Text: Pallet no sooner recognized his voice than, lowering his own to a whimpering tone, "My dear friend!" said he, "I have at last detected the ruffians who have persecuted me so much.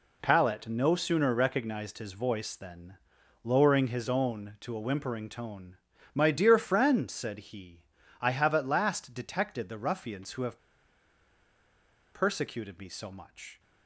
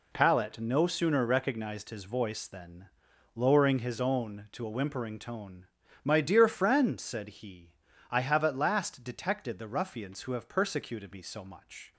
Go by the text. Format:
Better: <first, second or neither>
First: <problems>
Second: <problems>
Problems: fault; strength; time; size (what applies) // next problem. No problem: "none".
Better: second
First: pauses between "have" and "persecuted"; strong; at 10.5 s; 1.5 s long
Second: none